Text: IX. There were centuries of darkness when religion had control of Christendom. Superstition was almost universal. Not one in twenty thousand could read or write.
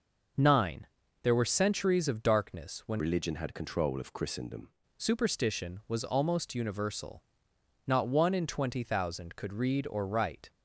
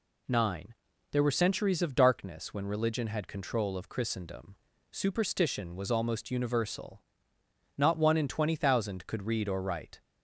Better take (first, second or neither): second